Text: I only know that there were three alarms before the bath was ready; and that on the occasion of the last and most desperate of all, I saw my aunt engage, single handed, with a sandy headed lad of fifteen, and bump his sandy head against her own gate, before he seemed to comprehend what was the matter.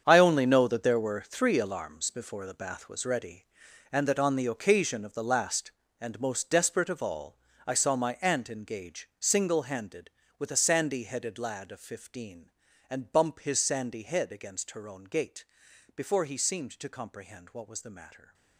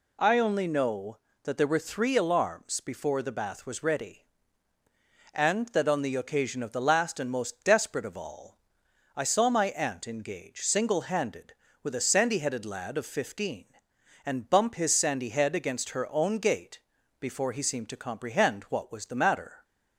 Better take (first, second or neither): second